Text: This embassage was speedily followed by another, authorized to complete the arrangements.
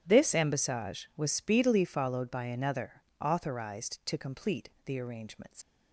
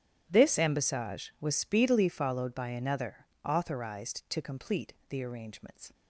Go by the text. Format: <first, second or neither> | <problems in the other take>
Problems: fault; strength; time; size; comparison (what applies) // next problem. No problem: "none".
second | starts louder than the rest; strong; until 1.0 s; 10 dB; strong in the second // pauses between "complete" and "the"; slight; at 4.6 s; 0.16 s long; slight in the second // leaves "arrangements" unfinished; at 5.6 s; 80 ms